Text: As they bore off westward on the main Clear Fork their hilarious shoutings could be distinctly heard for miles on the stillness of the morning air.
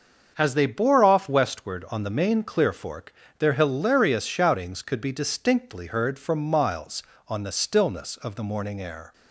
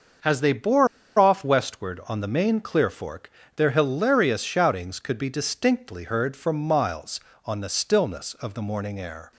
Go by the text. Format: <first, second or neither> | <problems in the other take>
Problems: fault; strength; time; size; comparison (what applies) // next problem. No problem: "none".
first | starts louder than the rest; until 1.5 s; 6.5 dB; also in the first // pauses between "bore" and "off"; slight; at 0.8 s; 0.31 s long // pauses between "Fork" and "their"; slight; at 3.2 s; 0.28 s long; slight in the first